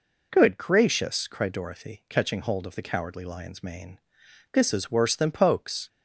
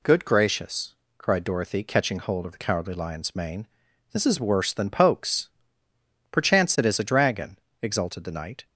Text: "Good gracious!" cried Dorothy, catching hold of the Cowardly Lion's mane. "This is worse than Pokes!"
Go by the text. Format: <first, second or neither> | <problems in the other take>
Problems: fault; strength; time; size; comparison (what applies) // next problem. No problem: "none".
first | goes on to say "Perchance it is a dragon exulted the Knight"; strong; from 6.3 s on; 2.3 s long